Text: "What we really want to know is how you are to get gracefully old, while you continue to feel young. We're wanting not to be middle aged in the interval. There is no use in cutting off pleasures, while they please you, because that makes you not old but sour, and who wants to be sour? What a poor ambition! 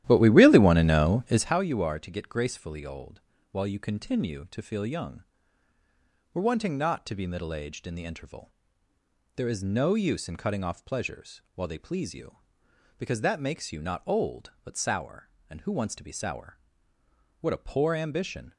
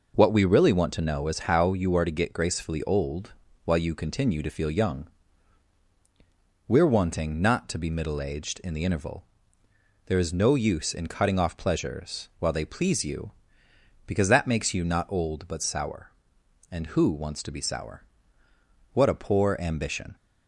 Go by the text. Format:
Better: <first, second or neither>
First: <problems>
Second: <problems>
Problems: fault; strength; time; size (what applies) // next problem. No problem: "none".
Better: second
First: starts louder than the rest; strong; until 1.6 s; 13 dB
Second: none